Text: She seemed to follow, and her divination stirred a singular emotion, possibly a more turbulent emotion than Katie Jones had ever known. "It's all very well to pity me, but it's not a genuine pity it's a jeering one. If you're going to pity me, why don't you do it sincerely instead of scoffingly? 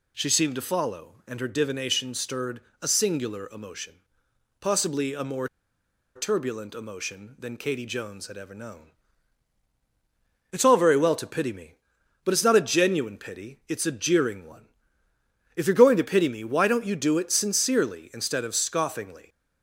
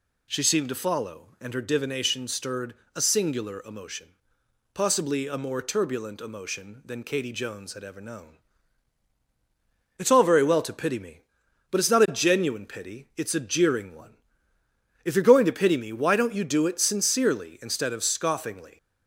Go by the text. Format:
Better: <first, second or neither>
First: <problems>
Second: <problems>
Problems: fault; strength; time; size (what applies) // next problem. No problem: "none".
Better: second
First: pauses between "stirred" and "a"; slight; at 2.6 s; 0.20 s long // pauses between "more" and "turbulent"; noticeable; at 5.4 s; 0.69 s long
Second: pauses between "stirred" and "a"; slight; at 2.7 s; 0.20 s long